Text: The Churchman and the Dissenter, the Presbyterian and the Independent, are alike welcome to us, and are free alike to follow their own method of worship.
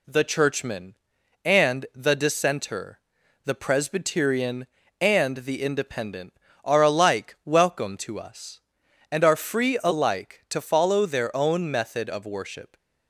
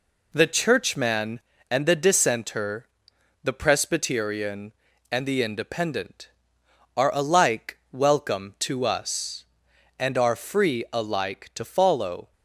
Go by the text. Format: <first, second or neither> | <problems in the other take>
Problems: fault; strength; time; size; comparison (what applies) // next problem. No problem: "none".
first | pauses between "alike" and "welcome"; slight; at 7.7 s; 0.16 s long // stops before "their own method of worship"; at 12.3 s